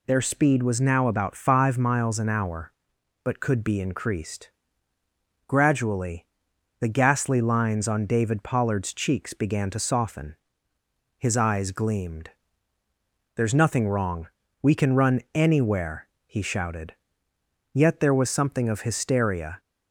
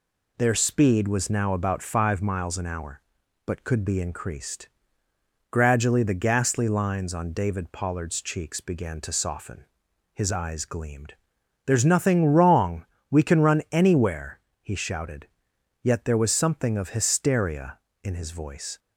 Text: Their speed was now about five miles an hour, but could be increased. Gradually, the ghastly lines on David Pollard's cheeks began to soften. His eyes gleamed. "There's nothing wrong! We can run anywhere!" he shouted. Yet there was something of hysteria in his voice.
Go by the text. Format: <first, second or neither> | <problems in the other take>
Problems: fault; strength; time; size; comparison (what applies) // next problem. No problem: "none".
second | stops before "in his voice"; at 19.5 s